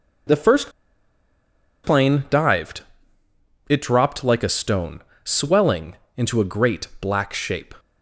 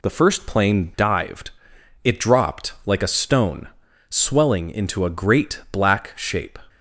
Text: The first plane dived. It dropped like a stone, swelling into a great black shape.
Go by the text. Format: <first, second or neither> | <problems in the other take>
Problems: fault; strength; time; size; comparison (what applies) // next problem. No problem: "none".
second | pauses between "first" and "plane"; at 0.7 s; 1.1 s long // pauses between "swelling" and "into"; slight; at 5.9 s; 0.18 s long